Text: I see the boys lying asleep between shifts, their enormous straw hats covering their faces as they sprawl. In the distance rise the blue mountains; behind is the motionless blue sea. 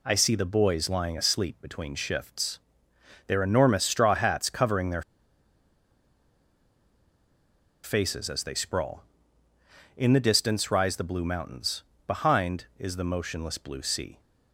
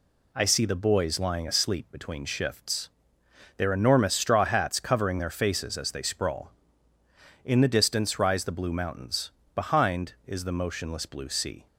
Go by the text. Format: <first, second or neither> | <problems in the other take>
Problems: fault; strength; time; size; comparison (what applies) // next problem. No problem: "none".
second | pauses between "their" and "faces"; strong; at 5.0 s; 2.8 s long